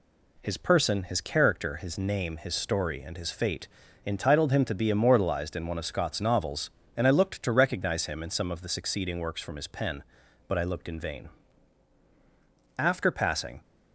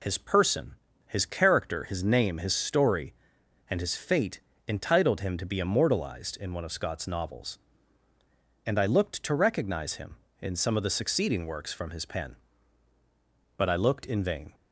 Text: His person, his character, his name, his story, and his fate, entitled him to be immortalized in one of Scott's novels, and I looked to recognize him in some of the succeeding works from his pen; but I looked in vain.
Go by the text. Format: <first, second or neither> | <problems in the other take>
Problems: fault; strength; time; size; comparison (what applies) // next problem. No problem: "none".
second | goes on to say "After passing"; noticeable; from 12.7 s on; 0.84 s long